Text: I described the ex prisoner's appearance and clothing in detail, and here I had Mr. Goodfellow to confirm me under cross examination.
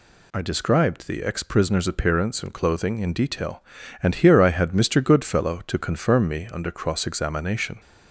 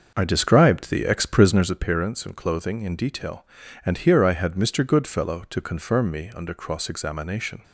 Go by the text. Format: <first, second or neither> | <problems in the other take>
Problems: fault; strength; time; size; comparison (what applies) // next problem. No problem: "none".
first | starts louder than the rest; noticeable; until 1.8 s; 6 dB